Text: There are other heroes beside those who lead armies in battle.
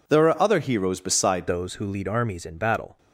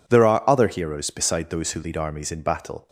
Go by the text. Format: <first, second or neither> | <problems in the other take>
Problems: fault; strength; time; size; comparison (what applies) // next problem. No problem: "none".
second | changes voice at "those"; from 1.4 s on; 1.5 s long